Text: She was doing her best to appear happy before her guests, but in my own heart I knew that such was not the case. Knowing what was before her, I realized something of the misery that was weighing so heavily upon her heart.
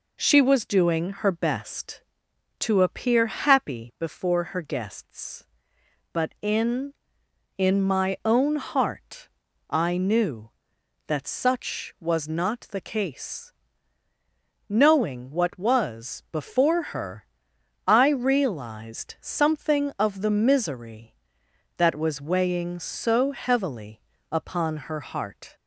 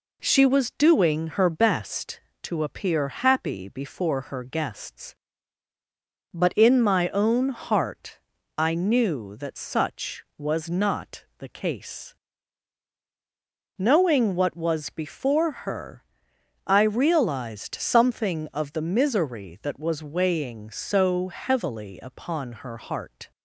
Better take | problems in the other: second | says "in" twice; at 7.5 s // pauses between "heart" and "I"; at 9.2 s; 0.40 s long; slight in the second // pauses between "heavily" and "upon"; slight; at 24.0 s; 0.28 s long // pauses between "upon" and "her"; slight; at 24.7 s; 0.16 s long

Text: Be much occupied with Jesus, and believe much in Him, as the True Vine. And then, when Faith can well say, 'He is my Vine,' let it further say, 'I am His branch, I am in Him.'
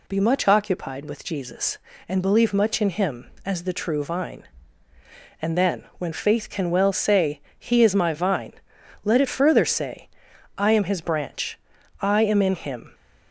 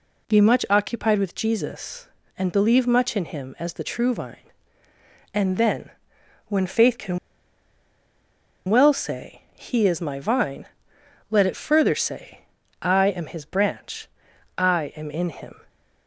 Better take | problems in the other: first | pauses between "can" and "well"; strong; at 7.1 s; 1.5 s long

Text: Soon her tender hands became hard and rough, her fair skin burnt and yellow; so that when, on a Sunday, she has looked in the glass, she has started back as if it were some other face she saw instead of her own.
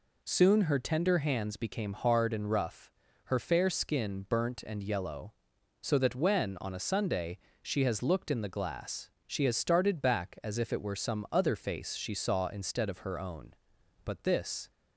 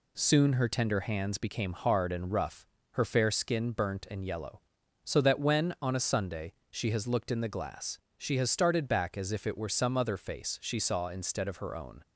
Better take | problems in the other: second | goes on to say "But this"; noticeable; from 14.0 s on; 0.66 s long

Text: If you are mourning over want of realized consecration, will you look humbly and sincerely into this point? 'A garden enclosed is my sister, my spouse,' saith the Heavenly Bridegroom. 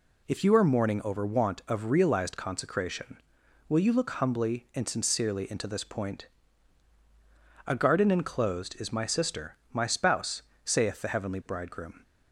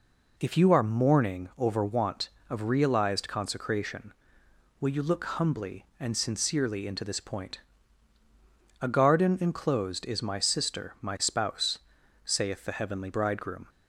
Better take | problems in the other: neither | none

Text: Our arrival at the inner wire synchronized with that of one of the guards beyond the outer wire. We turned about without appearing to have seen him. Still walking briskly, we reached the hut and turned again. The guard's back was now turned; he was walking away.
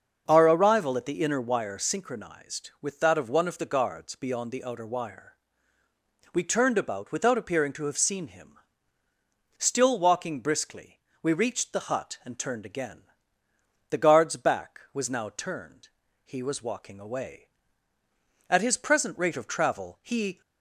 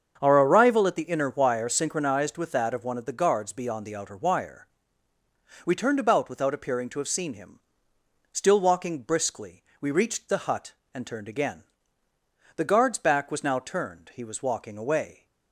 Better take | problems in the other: second | starts louder than the rest; until 1.2 s; 6.5 dB; also in the second // goes on to say "At his present rate of travel he"; strong; from 18.4 s on; 1.9 s long

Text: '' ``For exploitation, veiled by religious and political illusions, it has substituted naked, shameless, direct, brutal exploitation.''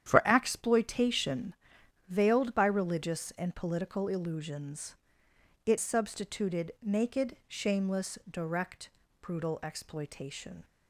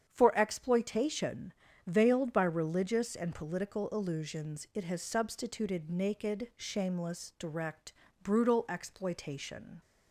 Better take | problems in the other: second | starts louder than the rest; strong; until 1.0 s; 9.5 dB; strong in the second // skips "has"; at 5.7 s

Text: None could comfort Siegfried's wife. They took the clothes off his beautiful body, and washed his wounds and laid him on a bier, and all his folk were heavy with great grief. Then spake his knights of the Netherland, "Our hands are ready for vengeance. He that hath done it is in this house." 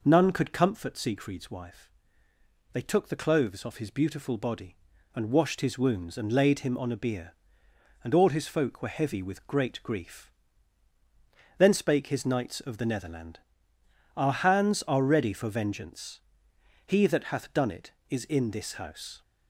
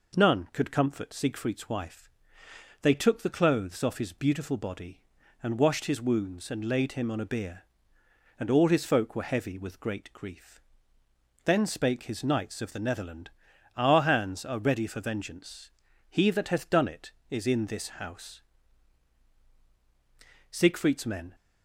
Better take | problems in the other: first | goes on to say "Siegfried's men"; noticeable; from 20.4 s on; 0.84 s long

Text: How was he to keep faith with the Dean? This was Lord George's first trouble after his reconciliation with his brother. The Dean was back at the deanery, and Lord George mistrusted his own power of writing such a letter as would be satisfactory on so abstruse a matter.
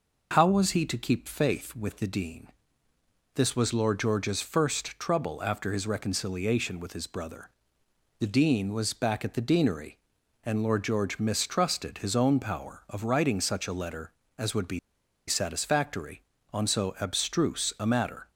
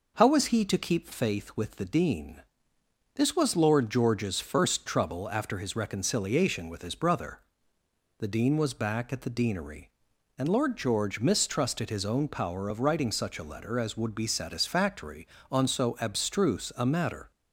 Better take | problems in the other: second | pauses between "be" and "satisfactory"; noticeable; at 14.7 s; 0.48 s long

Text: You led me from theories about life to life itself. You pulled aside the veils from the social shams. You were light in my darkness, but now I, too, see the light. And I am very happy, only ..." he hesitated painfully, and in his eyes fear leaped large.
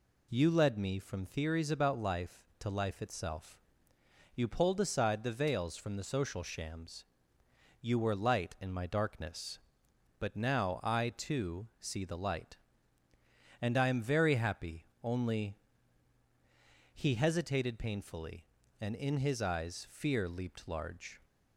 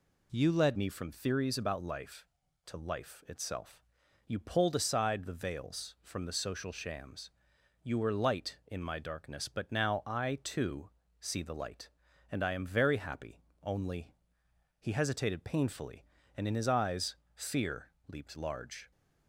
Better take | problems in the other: first | changes voice at "me"; from 0.7 s on; 18.2 s long // pauses between "eyes" and "fear"; slight; at 17.1 s; 0.18 s long // pauses between "fear" and "leaped"; slight; at 17.9 s; 0.16 s long

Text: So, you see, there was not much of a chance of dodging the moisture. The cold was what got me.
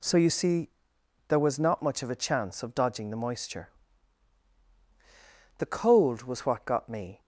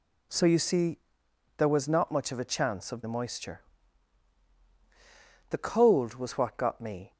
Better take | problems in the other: first | skips "dodging"; at 3.0 s

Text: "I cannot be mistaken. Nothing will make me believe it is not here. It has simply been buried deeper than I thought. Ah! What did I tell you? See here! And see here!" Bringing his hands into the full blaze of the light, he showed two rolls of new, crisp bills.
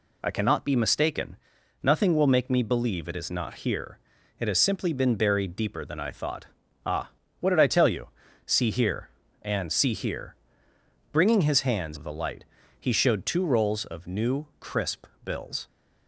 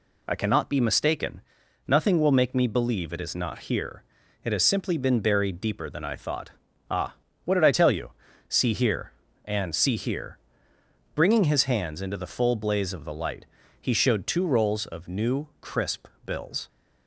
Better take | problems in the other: second | skips "into the full blaze"; at 11.9 s // pauses between "crisp" and "bills"; slight; at 15.0 s; 0.18 s long; slight in the second

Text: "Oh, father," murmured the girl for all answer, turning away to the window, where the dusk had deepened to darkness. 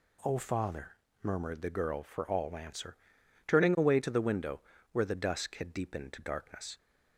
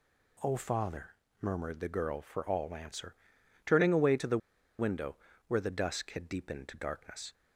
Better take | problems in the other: first | pauses between "the" and "window"; at 4.3 s; 0.40 s long

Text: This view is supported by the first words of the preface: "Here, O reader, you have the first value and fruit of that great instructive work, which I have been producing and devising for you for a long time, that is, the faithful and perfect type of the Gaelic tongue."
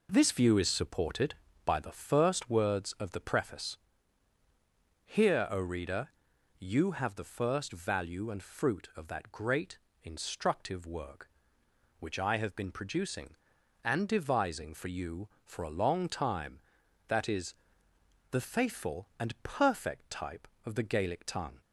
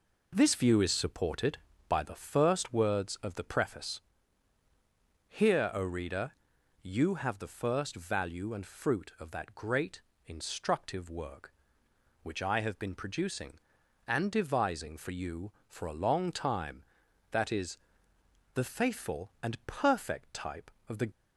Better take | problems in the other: first | pauses between "great" and "instructive"; slight; at 10.0 s; 0.24 s long; slight in the first // stops before "Gaelic tongue"; at 21.1 s

